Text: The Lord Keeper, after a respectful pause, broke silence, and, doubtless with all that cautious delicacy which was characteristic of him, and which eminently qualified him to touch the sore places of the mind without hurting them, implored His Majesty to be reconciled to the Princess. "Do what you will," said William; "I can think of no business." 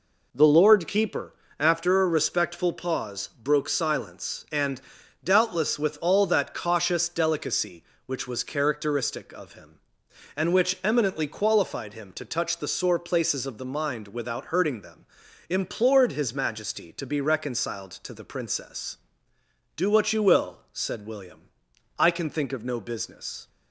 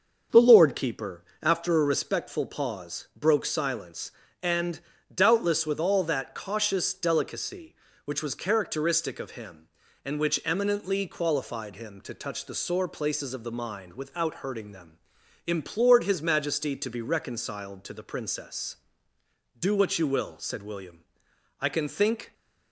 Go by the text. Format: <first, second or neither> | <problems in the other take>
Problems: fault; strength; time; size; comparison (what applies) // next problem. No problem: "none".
first | starts louder than the rest; until 1.4 s; 6.5 dB // stops before "of no business"; at 22.3 s